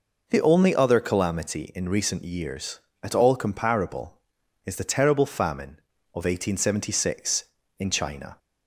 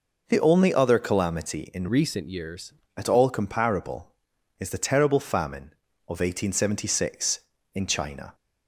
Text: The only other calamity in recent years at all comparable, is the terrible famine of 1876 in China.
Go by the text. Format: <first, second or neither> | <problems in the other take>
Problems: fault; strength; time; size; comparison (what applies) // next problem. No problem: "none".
first | changes voice from "recent" to "years"; from 1.8 to 2.7 s; 0.9 s long